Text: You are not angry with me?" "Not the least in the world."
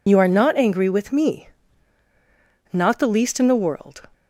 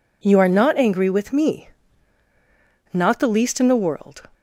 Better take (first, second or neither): second